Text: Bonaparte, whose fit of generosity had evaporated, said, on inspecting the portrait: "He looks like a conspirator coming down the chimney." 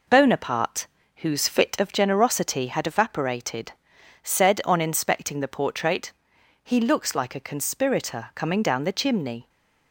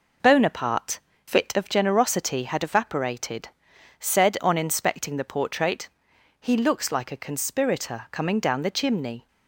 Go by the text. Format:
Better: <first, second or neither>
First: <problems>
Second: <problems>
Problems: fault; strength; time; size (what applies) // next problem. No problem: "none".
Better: first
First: none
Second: skips "whose"; at 1.1 s